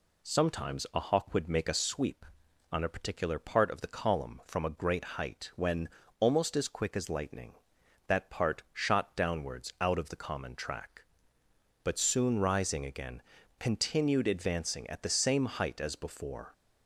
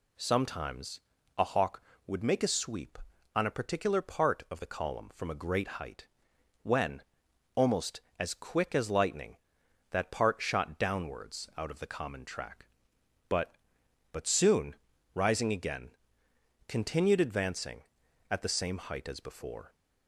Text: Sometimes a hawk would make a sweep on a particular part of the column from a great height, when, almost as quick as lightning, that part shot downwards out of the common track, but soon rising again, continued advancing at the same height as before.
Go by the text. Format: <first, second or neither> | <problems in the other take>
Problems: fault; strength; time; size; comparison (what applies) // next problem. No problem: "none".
first | pauses between "Sometimes" and "a"; slight; at 1.0 s; 0.34 s long // says "but" twice; at 14.1 s // pauses between "soon" and "rising"; at 14.7 s; 0.40 s long